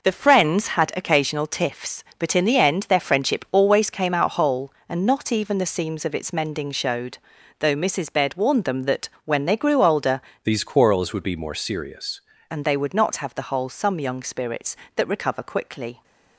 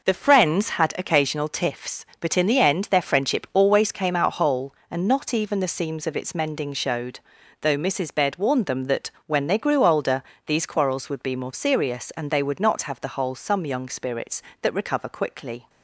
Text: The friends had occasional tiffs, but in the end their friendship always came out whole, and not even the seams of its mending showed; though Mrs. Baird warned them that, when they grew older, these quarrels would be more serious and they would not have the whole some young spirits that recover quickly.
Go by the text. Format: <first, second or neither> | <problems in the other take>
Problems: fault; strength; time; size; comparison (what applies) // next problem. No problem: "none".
second | changes voice from "these" to "serious"; from 10.4 to 12.2 s; 1.8 s long